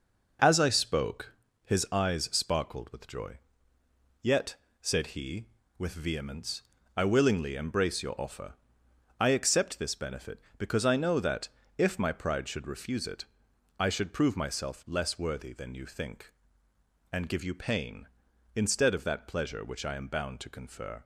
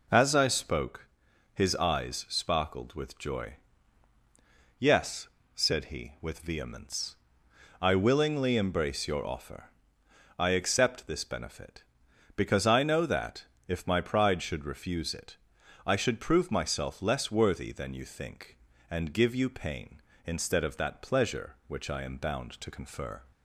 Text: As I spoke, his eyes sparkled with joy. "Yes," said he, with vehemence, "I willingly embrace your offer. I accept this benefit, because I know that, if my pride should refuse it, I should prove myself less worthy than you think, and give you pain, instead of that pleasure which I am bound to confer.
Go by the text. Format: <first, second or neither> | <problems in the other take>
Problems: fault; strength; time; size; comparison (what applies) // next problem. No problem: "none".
second | says "Yet" for "Yes"; at 4.2 s